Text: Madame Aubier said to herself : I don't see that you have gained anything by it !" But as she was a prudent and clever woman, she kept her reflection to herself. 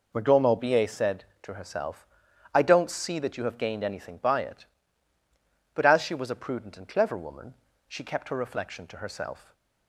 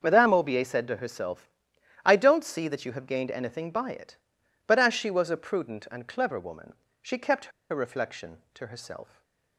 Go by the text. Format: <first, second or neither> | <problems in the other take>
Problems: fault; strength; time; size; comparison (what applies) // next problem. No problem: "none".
first | starts louder than the rest; until 1.0 s; 6.5 dB // pauses between "kept" and "her"; slight; at 7.5 s; 0.20 s long // stays silent after the last word; slight; from 9.0 s on; 0.5 s long